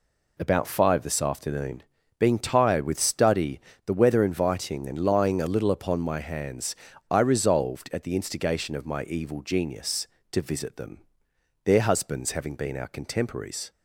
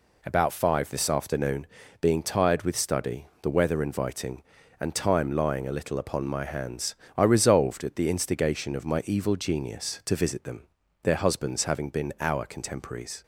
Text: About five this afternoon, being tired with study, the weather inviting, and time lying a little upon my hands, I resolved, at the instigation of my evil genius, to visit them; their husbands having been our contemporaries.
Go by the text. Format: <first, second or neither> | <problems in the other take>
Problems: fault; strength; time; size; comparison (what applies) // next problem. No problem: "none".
second | skips "time"; at 4.9 s